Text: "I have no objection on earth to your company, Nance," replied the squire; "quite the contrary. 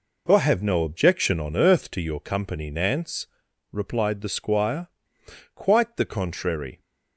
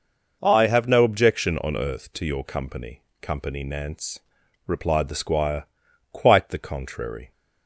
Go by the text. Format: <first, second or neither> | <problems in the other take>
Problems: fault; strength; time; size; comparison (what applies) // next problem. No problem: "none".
first | says "company" twice; at 3.2 s